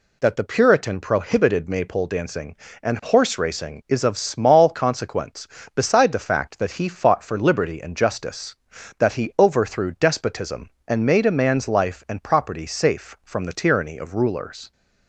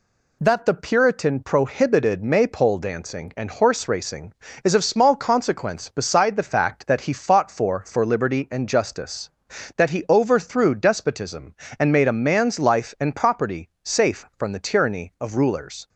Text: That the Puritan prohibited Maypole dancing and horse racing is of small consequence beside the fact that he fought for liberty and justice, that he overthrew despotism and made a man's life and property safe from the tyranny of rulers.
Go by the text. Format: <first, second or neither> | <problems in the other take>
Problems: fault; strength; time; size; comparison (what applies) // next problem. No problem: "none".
first | says "for" twice; at 7.8 s